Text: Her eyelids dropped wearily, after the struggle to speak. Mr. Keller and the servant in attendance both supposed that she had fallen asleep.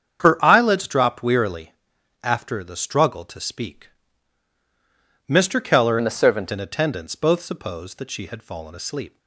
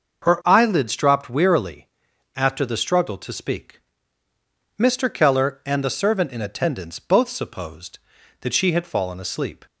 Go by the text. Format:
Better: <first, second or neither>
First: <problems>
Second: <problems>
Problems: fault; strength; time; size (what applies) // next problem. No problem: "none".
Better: second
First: starts louder than the rest; strong; until 1.2 s; 8 dB // changes voice from "and" to "servant"; from 5.9 to 6.5 s; 0.6 s long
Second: starts louder than the rest; noticeable; until 1.3 s; 6 dB